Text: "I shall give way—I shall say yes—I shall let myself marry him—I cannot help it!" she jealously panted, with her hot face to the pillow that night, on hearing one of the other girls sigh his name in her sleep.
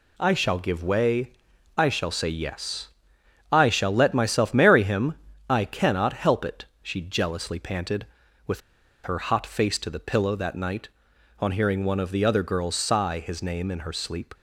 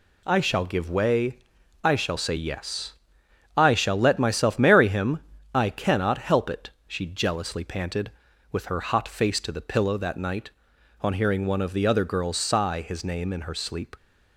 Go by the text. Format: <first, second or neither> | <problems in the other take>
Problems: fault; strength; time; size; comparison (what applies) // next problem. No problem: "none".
second | pauses between "with" and "her"; at 8.6 s; 0.43 s long